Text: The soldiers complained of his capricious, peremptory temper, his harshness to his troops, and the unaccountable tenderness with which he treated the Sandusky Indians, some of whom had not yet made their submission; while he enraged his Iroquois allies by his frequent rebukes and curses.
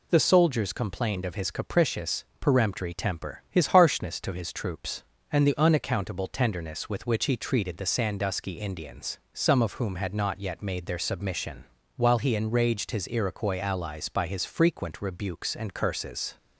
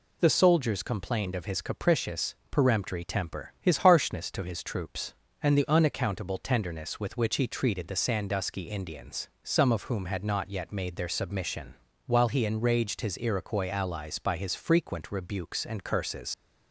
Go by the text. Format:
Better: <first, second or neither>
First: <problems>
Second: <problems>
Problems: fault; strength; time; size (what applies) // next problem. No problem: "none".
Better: first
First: none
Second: leaves "curses" unfinished; at 16.3 s; 130 ms